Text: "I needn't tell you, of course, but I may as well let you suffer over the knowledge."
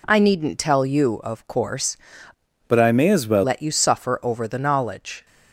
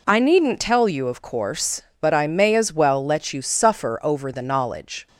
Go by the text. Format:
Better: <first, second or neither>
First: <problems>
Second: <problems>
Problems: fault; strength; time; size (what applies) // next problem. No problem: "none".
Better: second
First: changes voice from "but" to "well"; from 2.6 to 3.4 s; 0.8 s long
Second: none